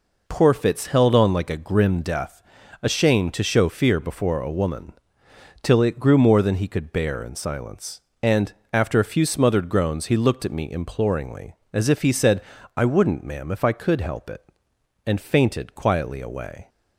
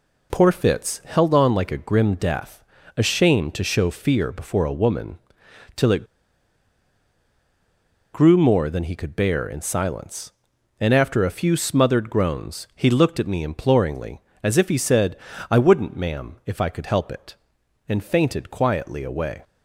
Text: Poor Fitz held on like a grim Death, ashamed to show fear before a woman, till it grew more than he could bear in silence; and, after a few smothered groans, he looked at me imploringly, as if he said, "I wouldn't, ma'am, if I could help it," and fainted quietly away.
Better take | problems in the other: first | pauses between "it" and "grew"; strong; at 6.0 s; 2.0 s long

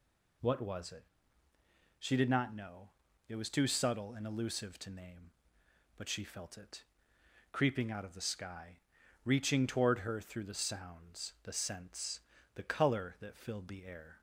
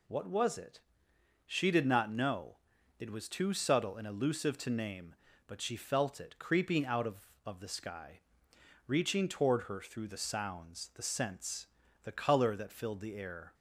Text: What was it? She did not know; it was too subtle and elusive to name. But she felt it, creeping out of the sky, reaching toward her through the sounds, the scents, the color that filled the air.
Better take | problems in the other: first | says "of" twice; at 7.4 s

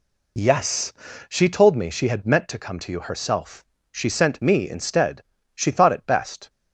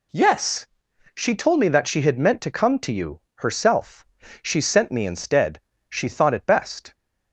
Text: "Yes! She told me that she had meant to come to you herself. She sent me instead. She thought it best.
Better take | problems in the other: second | skips "that"; at 1.8 s

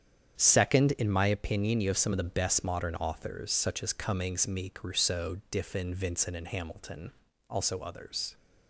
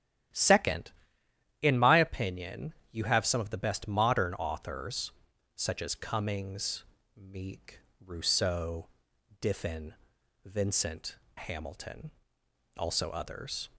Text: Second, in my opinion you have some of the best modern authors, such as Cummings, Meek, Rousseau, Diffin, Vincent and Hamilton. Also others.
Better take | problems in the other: first | starts louder than the rest; strong; until 2.0 s; 11.5 dB; strong in the first // pauses between "opinion" and "you"; slight; at 2.7 s; 0.20 s long // skips "and"; at 11.2 s

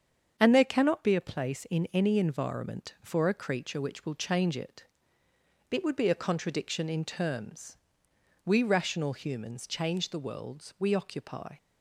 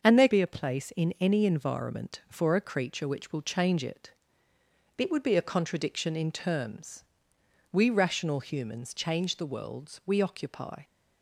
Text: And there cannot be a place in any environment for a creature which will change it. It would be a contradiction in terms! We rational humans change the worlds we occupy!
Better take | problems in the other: first | starts louder than the rest; until 1.1 s; 6.5 dB; strong in the first // skips "cannot"; at 0.2 s

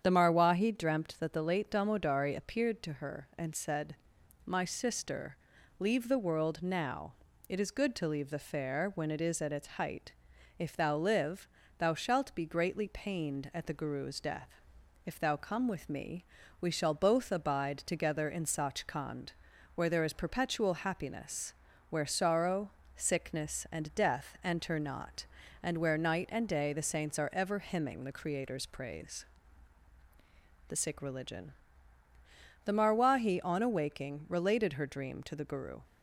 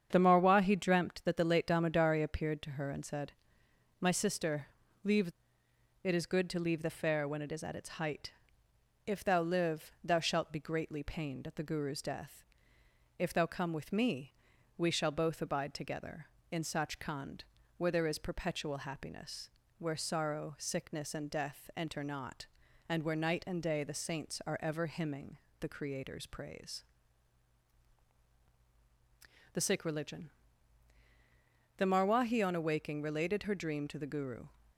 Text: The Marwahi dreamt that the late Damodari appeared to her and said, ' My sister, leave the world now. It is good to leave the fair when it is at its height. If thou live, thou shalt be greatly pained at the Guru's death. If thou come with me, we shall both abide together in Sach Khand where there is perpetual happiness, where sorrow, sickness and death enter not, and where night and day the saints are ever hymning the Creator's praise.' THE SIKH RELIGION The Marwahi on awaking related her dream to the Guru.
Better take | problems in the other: first | starts louder than the rest; strong; until 1.1 s; 8 dB; strong in the first // skips "the world now"; at 5.6 s // pauses between "Khand" and "where"; slight; at 17.4 s; 0.32 s long; also in the first // pauses between "hymning" and "the"; slight; at 25.3 s; 0.20 s long // pauses between "RELIGION" and "The"; strong; at 30.3 s; 1.4 s long; also in the first

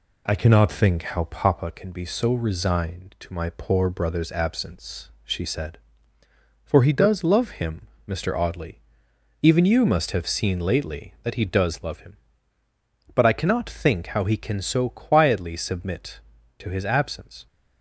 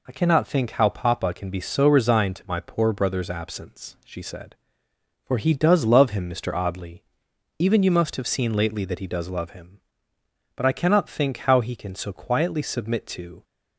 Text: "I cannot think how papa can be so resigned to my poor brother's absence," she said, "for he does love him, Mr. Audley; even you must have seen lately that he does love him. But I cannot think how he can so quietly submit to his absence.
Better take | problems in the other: first | stops before "his absence"; at 13.4 s

